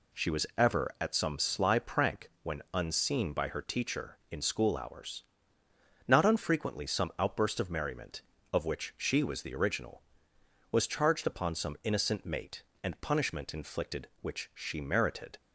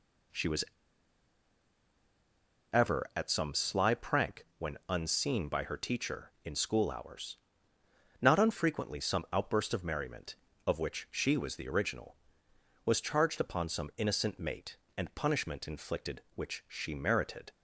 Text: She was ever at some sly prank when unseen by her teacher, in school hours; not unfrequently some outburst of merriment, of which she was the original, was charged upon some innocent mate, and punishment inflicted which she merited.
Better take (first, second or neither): first